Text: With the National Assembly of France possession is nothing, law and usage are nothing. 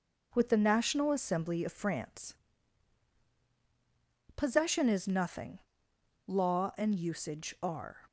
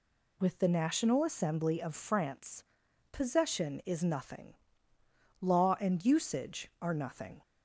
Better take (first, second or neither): second